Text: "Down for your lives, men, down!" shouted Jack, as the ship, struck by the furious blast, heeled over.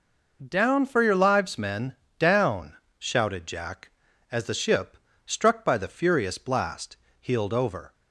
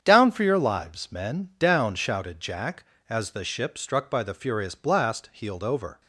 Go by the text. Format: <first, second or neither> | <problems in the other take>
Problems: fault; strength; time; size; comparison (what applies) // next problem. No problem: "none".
first | gets quieter; strong; throughout; 9.5 dB